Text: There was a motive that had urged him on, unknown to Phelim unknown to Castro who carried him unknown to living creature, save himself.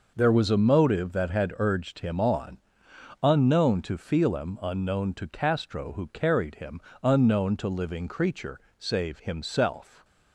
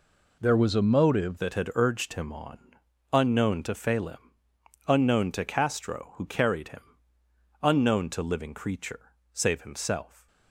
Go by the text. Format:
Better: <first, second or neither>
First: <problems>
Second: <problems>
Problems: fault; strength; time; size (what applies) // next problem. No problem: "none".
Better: first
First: pauses between "him" and "unknown"; slight; at 6.8 s; 0.20 s long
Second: changes voice at "that"; from 1.3 s on; 8.9 s long // pauses between "Phelim" and "unknown"; noticeable; at 4.1 s; 0.72 s long // pauses between "him" and "unknown"; noticeable; at 6.8 s; 0.80 s long